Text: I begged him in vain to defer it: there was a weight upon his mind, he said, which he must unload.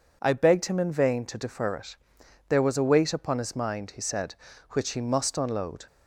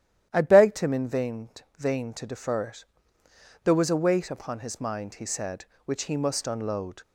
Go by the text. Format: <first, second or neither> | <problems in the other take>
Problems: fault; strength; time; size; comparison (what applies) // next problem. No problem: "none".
first | starts louder than the rest; strong; until 1.3 s; 11.5 dB // says "vain" twice; at 1.7 s